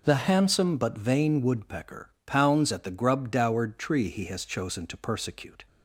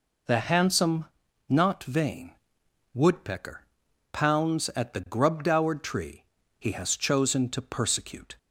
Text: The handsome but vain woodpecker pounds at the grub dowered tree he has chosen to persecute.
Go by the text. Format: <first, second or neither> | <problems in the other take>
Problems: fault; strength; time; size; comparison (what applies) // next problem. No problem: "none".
first | says "not" for "but"; at 1.4 s // pauses between "vain" and "woodpecker"; noticeable; at 2.3 s; 0.60 s long // pauses between "woodpecker" and "pounds"; noticeable; at 3.6 s; 0.48 s long; slight in the first // pauses between "tree" and "he"; slight; at 6.2 s; 0.36 s long